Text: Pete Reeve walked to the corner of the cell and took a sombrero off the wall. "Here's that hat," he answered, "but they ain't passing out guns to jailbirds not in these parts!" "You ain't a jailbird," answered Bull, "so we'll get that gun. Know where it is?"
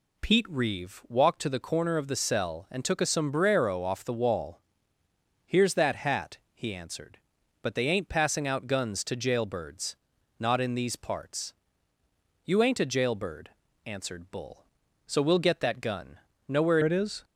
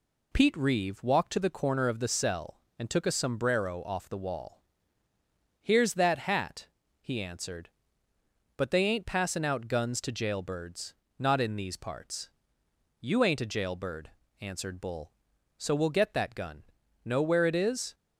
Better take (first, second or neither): second